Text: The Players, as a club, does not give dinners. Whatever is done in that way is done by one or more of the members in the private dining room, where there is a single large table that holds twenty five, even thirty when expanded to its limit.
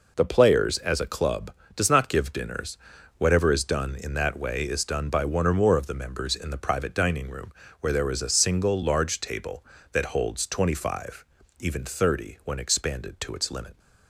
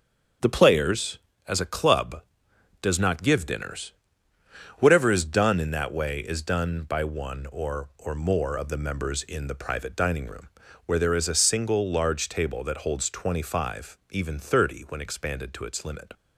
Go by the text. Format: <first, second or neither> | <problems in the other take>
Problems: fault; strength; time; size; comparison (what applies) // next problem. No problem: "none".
first | starts louder than the rest; until 1.7 s; 7 dB // says "or" twice; at 7.9 s